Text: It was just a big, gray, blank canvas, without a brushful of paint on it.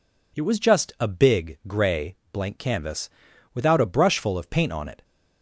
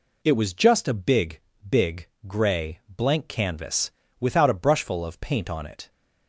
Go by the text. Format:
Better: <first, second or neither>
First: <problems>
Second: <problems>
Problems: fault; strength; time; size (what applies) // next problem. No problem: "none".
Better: first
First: none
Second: says "big" twice; at 1.6 s